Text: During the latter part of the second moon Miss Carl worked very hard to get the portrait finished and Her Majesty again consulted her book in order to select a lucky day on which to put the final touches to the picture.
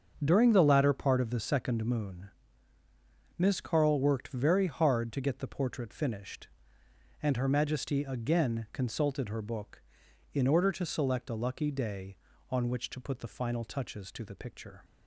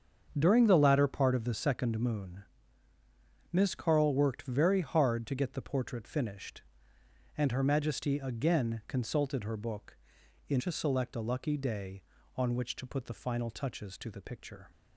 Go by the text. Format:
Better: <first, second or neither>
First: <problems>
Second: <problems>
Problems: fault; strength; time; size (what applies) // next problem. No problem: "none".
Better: first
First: starts louder than the rest; until 1.2 s; 7 dB // pauses between "moon" and "Miss"; at 2.2 s; 1.0 s long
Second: starts louder than the rest; strong; until 1.3 s; 7 dB // pauses between "moon" and "Miss"; at 2.4 s; 1.0 s long // skips "order"; at 10.5 s